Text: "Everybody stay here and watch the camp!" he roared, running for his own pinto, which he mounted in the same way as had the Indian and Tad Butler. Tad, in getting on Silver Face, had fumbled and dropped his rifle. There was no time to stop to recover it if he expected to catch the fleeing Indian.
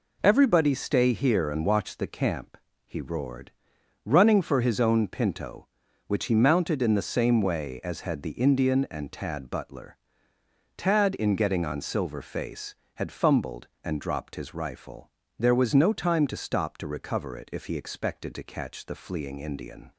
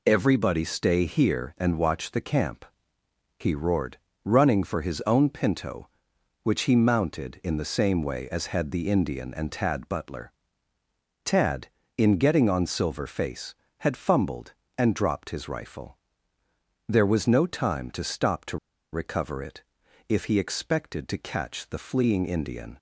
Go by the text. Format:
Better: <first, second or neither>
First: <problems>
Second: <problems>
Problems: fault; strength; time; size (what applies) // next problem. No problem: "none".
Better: first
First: none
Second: pauses between "to" and "recover"; slight; at 18.5 s; 0.34 s long // pauses between "it" and "if"; noticeable; at 19.6 s; 0.48 s long